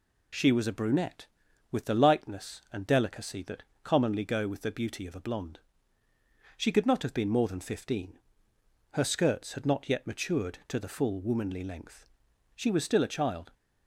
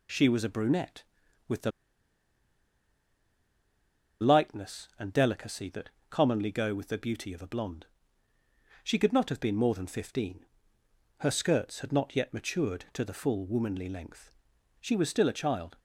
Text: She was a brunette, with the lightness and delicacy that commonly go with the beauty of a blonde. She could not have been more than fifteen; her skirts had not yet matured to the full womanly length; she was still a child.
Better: first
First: pauses between "that" and "commonly"; slight; at 3.6 s; 0.22 s long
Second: pauses between "the" and "lightness"; strong; at 1.7 s; 2.5 s long // pauses between "that" and "commonly"; slight; at 5.8 s; 0.22 s long

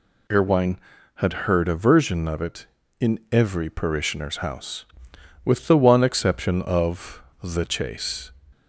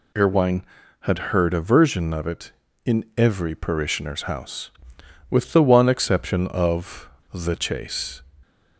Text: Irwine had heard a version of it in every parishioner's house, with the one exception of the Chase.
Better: neither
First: pauses between "of" and "the"; slight; at 7.2 s; 0.20 s long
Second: pauses between "of" and "the"; slight; at 7.0 s; 0.23 s long

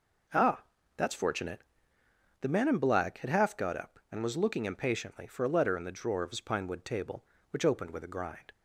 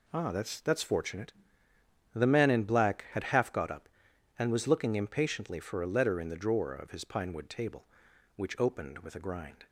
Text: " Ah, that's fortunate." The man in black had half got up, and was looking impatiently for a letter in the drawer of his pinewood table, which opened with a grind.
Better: first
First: none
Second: says "that's" twice; at 0.6 s

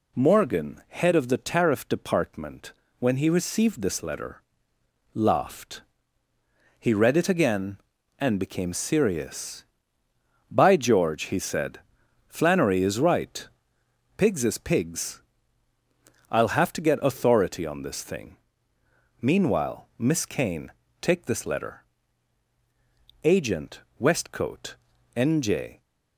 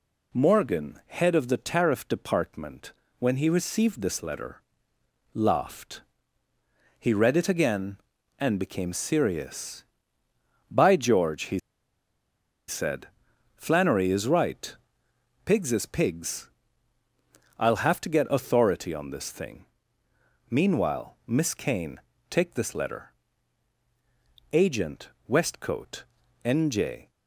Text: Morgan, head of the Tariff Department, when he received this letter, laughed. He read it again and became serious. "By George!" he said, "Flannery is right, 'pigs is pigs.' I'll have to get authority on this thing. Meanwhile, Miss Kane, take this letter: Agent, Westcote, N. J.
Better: first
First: none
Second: pauses between "he" and "said"; at 11.5 s; 1.1 s long

